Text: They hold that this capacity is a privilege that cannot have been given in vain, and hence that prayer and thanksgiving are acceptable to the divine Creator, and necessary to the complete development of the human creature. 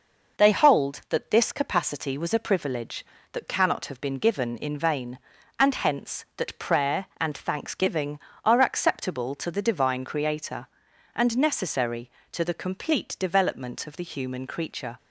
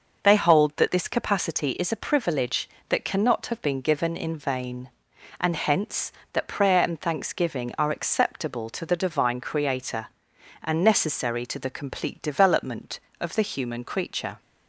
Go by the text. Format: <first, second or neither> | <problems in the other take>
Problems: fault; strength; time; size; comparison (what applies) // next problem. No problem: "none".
second | says "was" for "is"; at 2.1 s